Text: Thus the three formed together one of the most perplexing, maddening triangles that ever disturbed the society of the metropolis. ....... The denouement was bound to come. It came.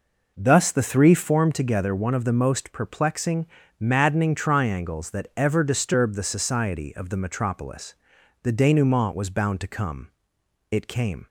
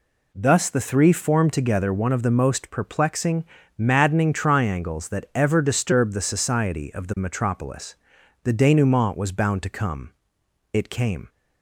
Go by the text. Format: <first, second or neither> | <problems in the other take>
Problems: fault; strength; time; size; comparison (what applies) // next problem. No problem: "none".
second | starts louder than the rest; noticeable; until 1.4 s; 5 dB